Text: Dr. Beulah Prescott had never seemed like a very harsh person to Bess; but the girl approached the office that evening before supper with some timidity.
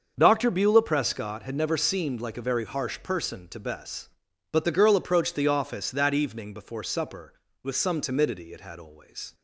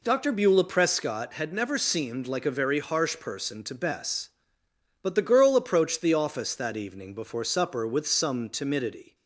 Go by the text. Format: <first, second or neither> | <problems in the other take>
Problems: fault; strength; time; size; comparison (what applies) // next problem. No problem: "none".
second | starts louder than the rest; until 1.1 s; 6.5 dB // goes on to say "It had always"; noticeable; from 8.5 s on; 0.80 s long